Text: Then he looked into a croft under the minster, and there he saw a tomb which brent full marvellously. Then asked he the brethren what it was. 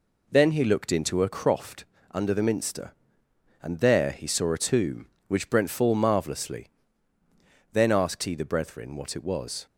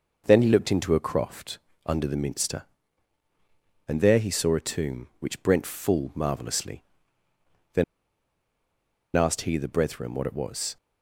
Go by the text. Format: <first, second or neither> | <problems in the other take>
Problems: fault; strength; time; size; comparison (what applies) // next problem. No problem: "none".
first | pauses between "croft" and "under"; slight; at 1.5 s; 0.26 s long; slight in the first // pauses between "Then" and "asked"; strong; at 7.8 s; 1.3 s long